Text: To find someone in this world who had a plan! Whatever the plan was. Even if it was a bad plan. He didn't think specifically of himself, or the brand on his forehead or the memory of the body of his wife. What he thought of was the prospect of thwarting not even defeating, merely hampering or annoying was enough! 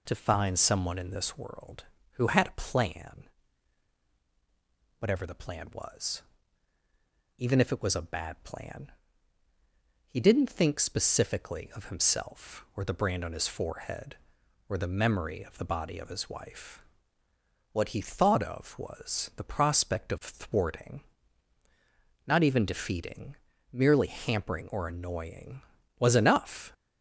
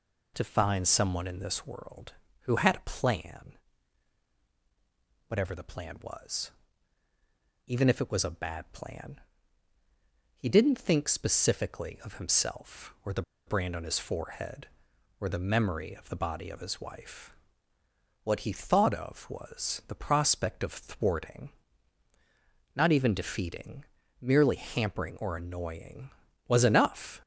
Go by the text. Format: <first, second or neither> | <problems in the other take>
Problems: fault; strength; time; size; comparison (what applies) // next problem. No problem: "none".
first | pauses between "the" and "brand"; slight; at 13.2 s; 0.25 s long // pauses between "thwarting" and "not"; strong; at 21.4 s; 1.2 s long; strong in the first